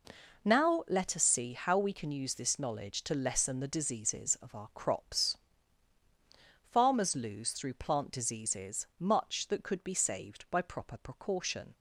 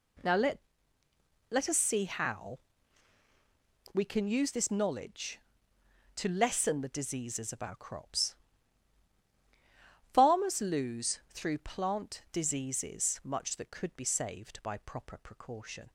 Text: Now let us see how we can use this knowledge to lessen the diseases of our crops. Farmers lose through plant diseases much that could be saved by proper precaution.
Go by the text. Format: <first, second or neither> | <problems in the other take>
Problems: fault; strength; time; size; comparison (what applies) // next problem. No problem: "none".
first | says "let" twice; at 1.4 s // pauses between "how" and "we"; strong; at 2.5 s; 1.3 s long